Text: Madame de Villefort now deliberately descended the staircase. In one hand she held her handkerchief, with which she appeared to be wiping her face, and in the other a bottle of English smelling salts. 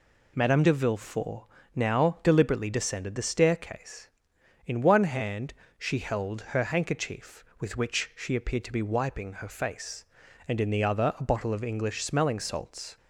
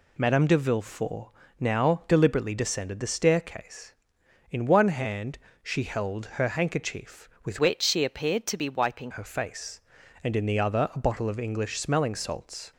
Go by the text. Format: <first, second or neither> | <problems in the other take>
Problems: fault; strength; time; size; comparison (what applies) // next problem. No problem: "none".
first | pauses between "Villefort" and "now"; slight; at 1.2 s; 0.30 s long; slight in the first // pauses between "hand" and "she"; slight; at 5.3 s; 0.24 s long; slight in the first // pauses between "held" and "her"; slight; at 6.2 s; 0.16 s long; slight in the first // changes voice from "which" to "wiping"; from 7.5 to 9.1 s; 1.6 s long